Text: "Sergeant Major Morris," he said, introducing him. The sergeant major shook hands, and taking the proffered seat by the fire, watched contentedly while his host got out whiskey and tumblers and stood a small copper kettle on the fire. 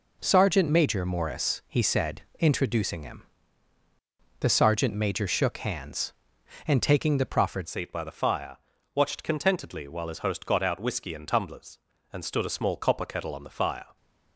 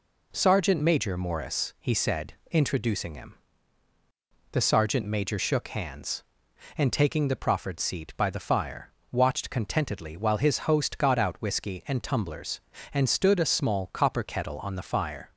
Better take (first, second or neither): second